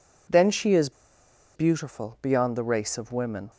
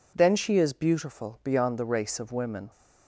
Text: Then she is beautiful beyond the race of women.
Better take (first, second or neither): second